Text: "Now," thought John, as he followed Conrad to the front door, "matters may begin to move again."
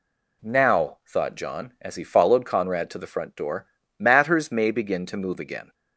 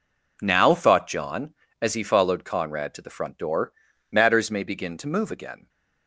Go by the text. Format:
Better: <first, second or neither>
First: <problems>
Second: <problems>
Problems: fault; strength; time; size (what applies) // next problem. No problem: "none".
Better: neither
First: none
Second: none